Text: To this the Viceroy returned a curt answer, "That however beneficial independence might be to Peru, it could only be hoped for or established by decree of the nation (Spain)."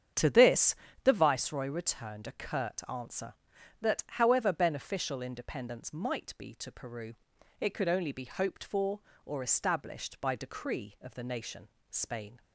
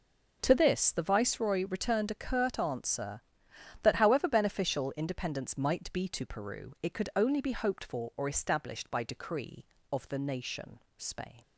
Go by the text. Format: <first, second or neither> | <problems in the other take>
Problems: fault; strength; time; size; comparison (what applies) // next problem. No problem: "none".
second | starts louder than the rest; strong; until 1.3 s; 8 dB // pauses between "this" and "the"; slight; at 0.7 s; 0.28 s long